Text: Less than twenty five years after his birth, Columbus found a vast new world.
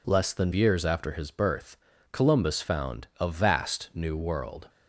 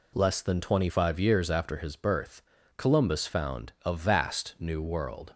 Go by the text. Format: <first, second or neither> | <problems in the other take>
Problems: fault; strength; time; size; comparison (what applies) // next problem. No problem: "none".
second | skips "twenty five"; at 0.5 s